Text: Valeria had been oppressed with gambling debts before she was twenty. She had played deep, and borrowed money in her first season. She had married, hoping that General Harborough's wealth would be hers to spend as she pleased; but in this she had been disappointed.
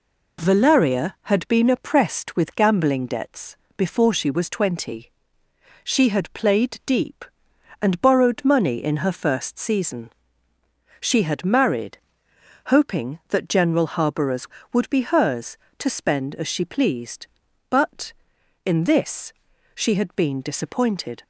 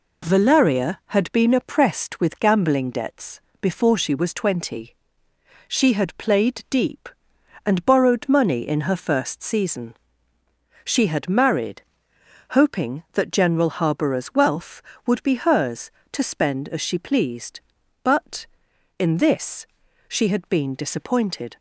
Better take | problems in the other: second | pauses between "debts" and "before"; slight; at 3.5 s; 0.18 s long; slight in the second // skips "wealth"; at 14.6 s // pauses between "this" and "she"; at 19.3 s; 0.40 s long; also in the second

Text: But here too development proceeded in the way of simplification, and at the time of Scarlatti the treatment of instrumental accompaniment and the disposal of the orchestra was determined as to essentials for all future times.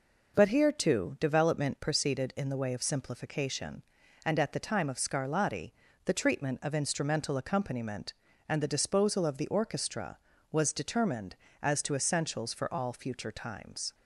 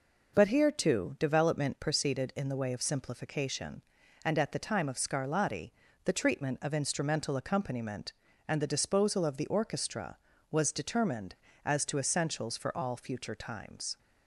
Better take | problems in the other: neither | pauses between "Scarlatti" and "the"; slight; the same in both

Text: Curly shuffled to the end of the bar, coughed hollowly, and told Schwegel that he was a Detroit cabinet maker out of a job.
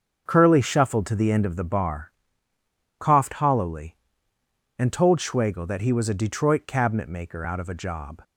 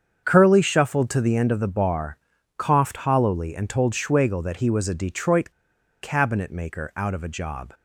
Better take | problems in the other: first | starts louder than the rest; strong; until 1.2 s; 7.5 dB; also in the first // pauses between "Detroit" and "cabinet"; noticeable; at 5.5 s; 0.50 s long

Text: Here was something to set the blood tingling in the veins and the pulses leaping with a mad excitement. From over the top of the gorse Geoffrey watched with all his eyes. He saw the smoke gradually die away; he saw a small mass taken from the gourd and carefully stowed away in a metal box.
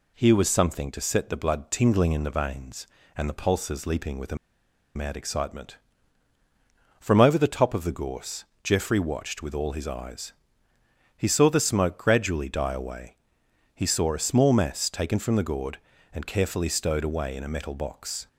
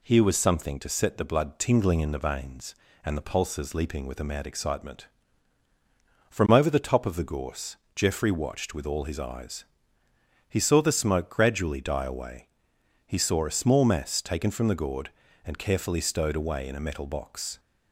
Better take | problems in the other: second | pauses between "a" and "mad"; noticeable; at 4.3 s; 0.59 s long // pauses between "gorse" and "Geoffrey"; slight; at 8.4 s; 0.18 s long; slight in the second

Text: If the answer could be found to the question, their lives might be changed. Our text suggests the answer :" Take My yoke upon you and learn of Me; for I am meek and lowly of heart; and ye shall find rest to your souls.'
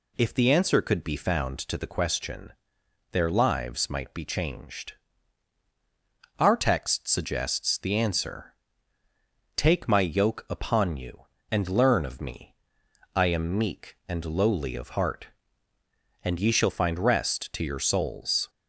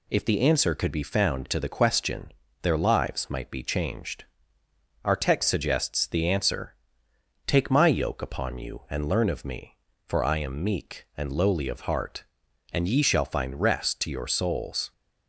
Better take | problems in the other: second | skips "for"; at 12.8 s

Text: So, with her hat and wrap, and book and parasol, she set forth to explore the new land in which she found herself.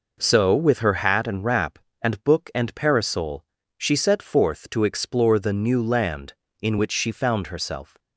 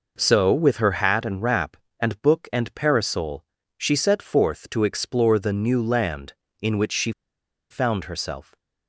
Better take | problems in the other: first | pauses between "she" and "found"; noticeable; at 7.1 s; 0.59 s long

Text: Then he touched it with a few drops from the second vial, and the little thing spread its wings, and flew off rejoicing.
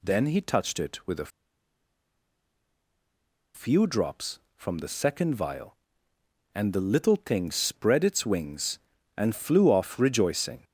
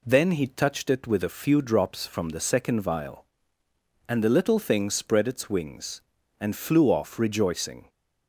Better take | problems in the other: second | pauses between "a" and "few"; strong; at 1.3 s; 2.2 s long

